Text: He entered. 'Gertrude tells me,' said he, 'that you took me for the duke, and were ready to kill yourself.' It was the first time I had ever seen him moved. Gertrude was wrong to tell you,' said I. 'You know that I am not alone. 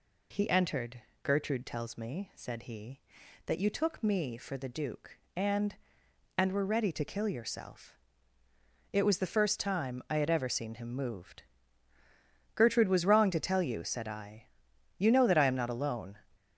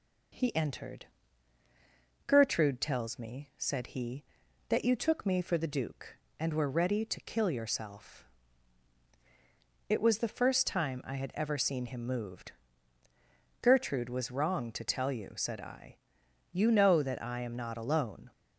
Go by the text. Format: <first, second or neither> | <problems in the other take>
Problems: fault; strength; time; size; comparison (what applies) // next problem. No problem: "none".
second | says "and" twice; at 6.3 s